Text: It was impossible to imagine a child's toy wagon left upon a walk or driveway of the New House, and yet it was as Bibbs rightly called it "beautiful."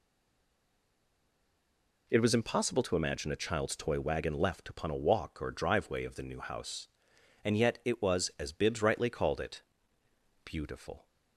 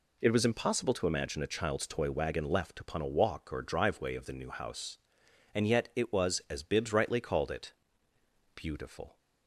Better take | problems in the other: second | stays silent before the first word; noticeable; until 2.0 s; 2.0 s long // pauses between "it" and "beautiful"; noticeable; at 9.6 s; 0.82 s long; noticeable in the second

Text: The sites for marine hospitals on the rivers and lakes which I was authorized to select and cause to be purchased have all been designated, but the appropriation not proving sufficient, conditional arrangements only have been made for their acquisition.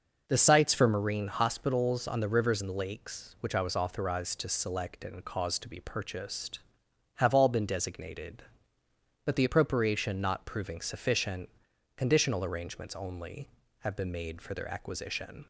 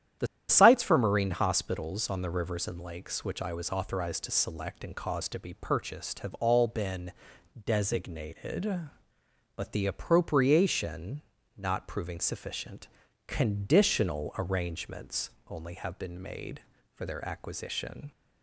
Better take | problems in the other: first | starts louder than the rest; strong; until 1.4 s; 10.5 dB // pauses between "The" and "sites"; slight; at 0.2 s; 0.24 s long // pauses between "been" and "designated"; noticeable; at 7.1 s; 0.54 s long // pauses between "appropriation" and "not"; slight; at 11.2 s; 0.34 s long // pauses between "arrangements" and "only"; slight; at 15.3 s; 0.16 s long

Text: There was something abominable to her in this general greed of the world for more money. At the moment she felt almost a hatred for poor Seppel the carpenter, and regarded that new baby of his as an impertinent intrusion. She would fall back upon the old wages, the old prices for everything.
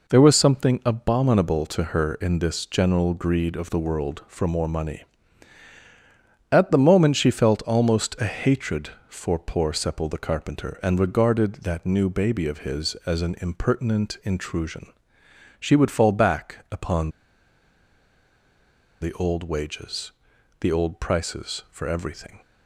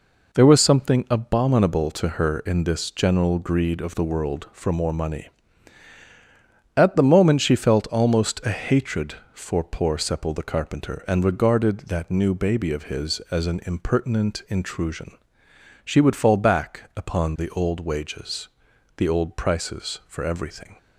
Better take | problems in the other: second | pauses between "upon" and "the"; strong; at 17.0 s; 1.9 s long

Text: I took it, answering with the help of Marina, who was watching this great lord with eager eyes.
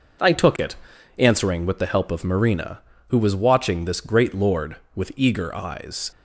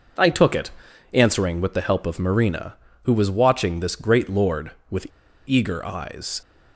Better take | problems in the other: first | pauses between "with" and "eager"; at 5.0 s; 0.41 s long

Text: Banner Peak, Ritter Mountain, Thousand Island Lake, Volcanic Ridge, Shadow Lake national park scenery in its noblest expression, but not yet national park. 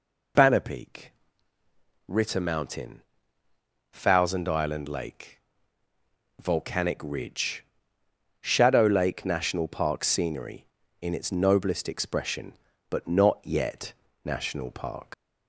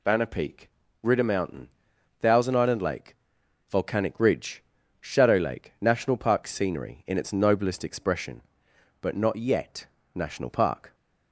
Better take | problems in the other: second | pauses between "yet" and "national"; slight; at 13.9 s; 0.32 s long; slight in the second // leaves "park" unfinished; at 15.1 s; 80 ms

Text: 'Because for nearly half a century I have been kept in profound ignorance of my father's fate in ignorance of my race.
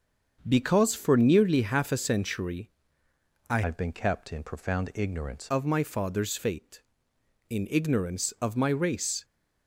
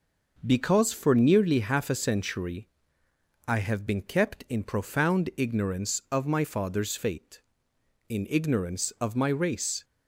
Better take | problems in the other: second | starts louder than the rest; until 1.4 s; 6.5 dB // pauses between "century" and "I"; noticeable; at 2.6 s; 0.80 s long; noticeable in the second // changes voice from "have" to "ignorance"; from 3.6 to 5.4 s; 1.8 s long

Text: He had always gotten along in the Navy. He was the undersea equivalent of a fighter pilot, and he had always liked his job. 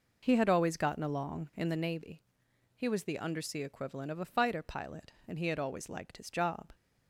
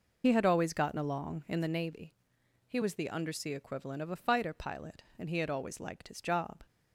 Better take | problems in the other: first | loses the start of "He"; at 0.2 s; 55 ms

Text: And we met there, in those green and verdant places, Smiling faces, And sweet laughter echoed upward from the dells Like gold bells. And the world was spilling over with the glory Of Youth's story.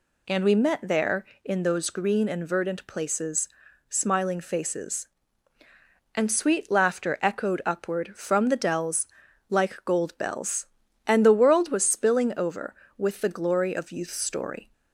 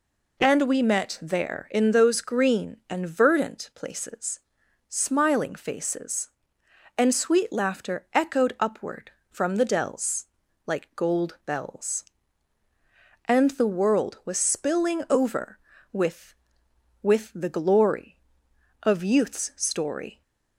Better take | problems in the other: first | pauses between "dells" and "Like"; at 10.2 s; 0.40 s long; also in the first // says "with" twice; at 17.0 s

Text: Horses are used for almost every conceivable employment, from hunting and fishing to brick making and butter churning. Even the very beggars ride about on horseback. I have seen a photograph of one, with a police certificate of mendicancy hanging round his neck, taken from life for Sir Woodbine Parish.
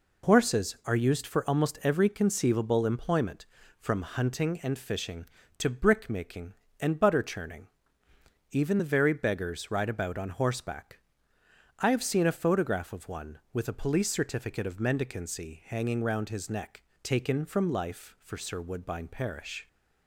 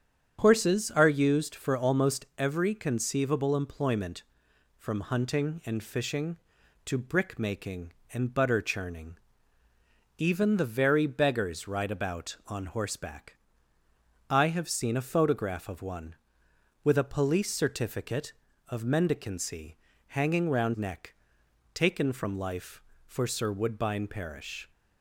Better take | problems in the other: first | starts louder than the rest; strong; until 1.4 s; 8 dB // pauses between "mendicancy" and "hanging"; slight; at 19.7 s; 0.32 s long // skips "his"; at 20.7 s

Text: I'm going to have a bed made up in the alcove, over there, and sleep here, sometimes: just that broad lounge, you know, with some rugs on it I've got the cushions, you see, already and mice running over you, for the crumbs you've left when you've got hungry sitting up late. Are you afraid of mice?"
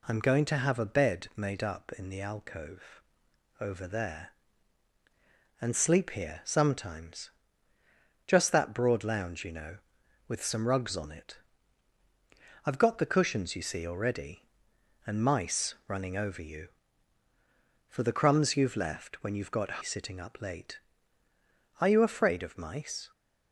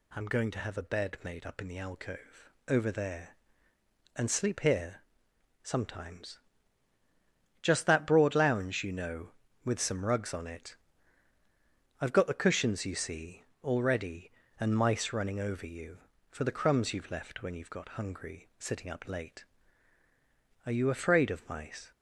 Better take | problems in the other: second | pauses between "it" and "I've"; strong; at 11.3 s; 1.2 s long; strong in the second // skips "hungry"; at 19.8 s

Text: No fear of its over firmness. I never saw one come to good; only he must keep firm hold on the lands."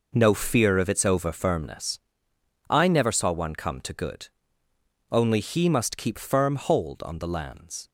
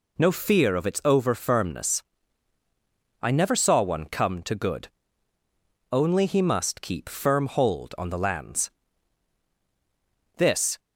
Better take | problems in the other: first | goes on to say "This"; slight; from 10.3 s on; 0.42 s long

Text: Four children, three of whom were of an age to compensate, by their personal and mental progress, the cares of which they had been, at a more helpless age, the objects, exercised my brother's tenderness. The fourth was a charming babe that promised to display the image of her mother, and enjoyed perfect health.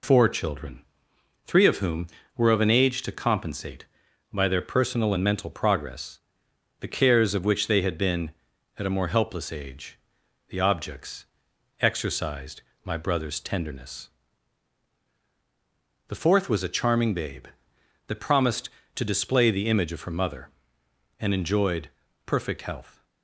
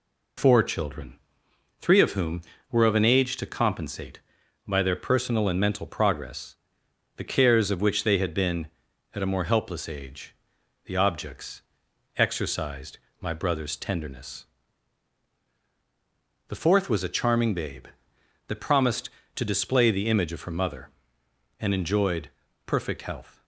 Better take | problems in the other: neither | pauses between "exercised" and "my"; slight; the same in both // pauses between "enjoyed" and "perfect"; slight; the same in both

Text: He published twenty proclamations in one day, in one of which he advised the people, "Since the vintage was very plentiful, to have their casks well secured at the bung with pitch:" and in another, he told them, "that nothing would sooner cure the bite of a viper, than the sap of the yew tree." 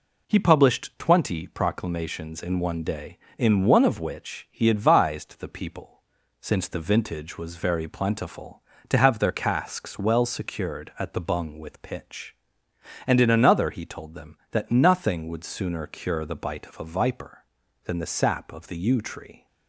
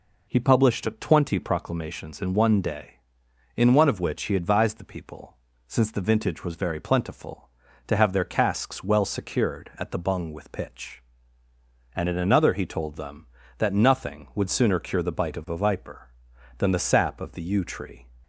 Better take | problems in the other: neither | none

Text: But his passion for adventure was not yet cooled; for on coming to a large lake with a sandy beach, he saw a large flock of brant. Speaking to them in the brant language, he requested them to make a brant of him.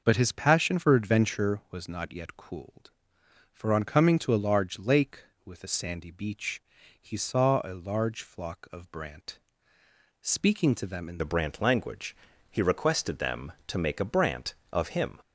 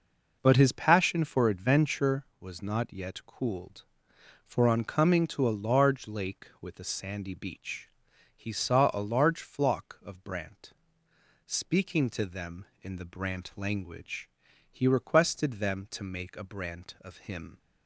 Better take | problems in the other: second | changes voice at "the"; from 11.1 s on; 4.0 s long

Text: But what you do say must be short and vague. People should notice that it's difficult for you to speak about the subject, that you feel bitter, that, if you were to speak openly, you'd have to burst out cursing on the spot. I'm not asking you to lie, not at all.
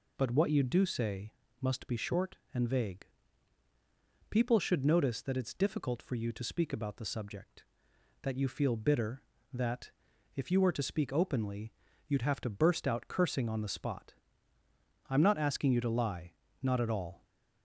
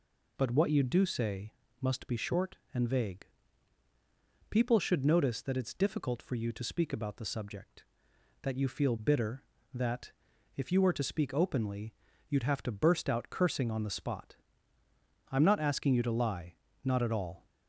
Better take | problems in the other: neither | pauses between "say" and "must"; slight; the same in both

